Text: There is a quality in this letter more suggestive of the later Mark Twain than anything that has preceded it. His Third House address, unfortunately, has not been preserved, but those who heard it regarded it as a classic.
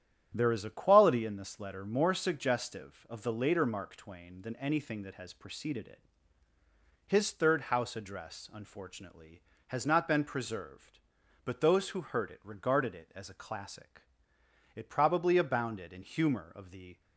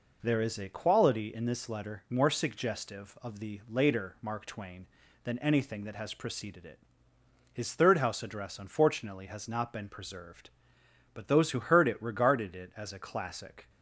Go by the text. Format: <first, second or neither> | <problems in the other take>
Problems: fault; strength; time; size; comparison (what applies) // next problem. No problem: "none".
second | starts louder than the rest; strong; until 1.3 s; 10 dB // goes on to say "It probably abounded in humor of the"; strong; from 14.7 s on; 2.2 s long